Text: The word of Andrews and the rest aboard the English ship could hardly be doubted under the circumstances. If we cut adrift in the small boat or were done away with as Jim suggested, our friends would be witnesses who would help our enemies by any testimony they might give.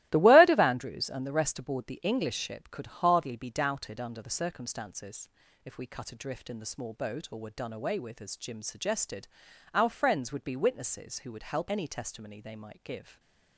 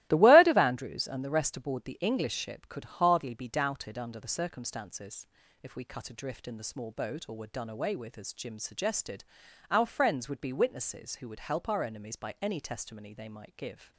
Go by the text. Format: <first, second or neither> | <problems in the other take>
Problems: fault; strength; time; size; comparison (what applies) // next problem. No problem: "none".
second | starts louder than the rest; strong; until 1.1 s; 16.5 dB; strong in the second // skips "our enemies by"; at 11.6 s